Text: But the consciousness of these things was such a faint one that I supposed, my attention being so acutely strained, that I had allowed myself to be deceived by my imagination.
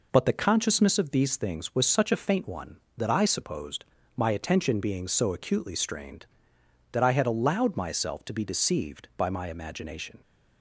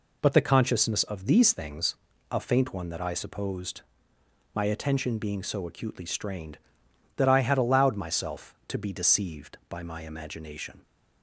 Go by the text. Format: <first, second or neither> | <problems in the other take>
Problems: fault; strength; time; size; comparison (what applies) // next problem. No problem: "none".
first | skips "was such"; at 2.1 s